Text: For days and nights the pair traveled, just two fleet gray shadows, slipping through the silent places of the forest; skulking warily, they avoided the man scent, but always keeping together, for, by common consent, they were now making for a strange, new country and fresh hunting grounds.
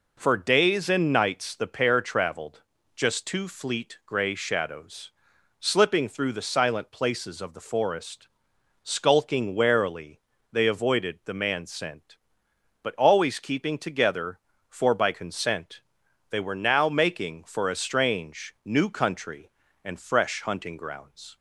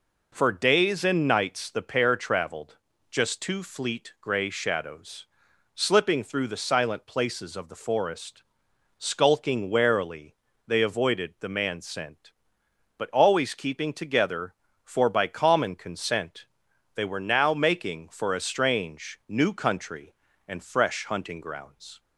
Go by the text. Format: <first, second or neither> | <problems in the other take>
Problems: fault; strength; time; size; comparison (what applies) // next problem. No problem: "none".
second | skips "common"; at 15.1 s